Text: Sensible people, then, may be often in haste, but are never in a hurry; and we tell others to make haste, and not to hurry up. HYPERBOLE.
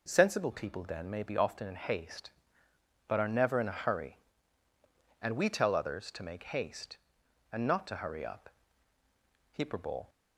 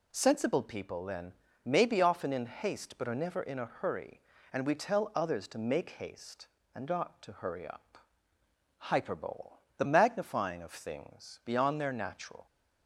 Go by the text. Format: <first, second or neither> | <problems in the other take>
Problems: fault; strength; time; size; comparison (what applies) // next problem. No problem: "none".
first | goes on to say "The magnifying of things beyond their natural"; strong; from 9.7 s on; 2.6 s long